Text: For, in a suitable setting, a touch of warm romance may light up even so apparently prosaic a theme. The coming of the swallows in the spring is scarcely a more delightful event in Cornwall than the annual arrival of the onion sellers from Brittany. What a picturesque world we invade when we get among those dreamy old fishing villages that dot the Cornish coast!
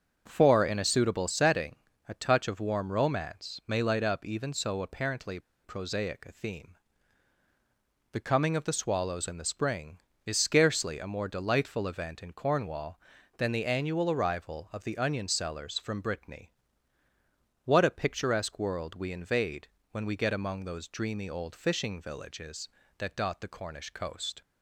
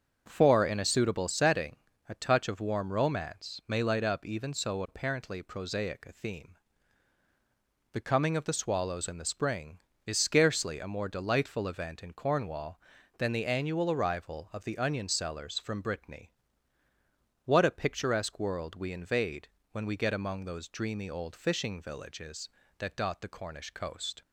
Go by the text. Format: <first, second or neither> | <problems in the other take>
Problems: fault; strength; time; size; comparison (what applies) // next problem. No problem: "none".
second | starts louder than the rest; until 1.2 s; 6.5 dB; also in the second // pauses between "apparently" and "prosaic"; slight; at 5.3 s; 0.25 s long // pauses between "invade" and "when"; slight; at 19.6 s; 0.24 s long; slight in the second